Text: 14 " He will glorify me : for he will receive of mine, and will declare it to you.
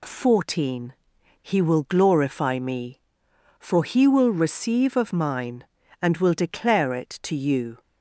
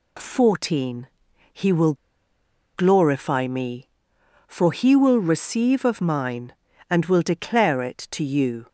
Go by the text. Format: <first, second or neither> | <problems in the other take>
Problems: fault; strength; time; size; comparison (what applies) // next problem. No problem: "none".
first | pauses between "will" and "glorify"; noticeable; at 1.9 s; 0.80 s long